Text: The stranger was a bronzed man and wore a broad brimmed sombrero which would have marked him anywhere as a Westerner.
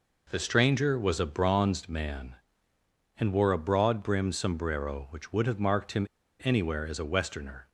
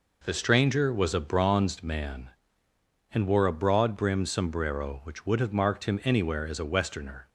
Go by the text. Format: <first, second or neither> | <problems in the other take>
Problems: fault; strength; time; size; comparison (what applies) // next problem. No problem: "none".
second | pauses between "him" and "anywhere"; at 6.0 s; 0.38 s long